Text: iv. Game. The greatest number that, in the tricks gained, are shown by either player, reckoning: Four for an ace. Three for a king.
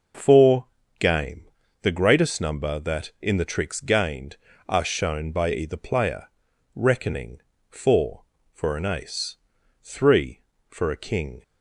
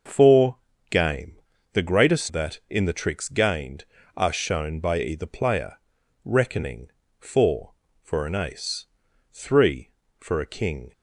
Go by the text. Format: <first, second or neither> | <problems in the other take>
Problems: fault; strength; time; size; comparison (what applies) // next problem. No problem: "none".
first | starts louder than the rest; noticeable; until 1.7 s; 6 dB // skips "number"; at 2.2 s